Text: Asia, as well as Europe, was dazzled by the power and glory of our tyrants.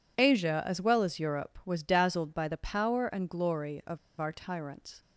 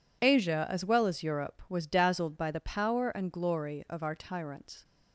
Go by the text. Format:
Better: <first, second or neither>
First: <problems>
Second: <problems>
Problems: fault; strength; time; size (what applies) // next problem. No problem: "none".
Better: second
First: pauses between "of" and "our"; slight; at 3.9 s; 0.20 s long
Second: none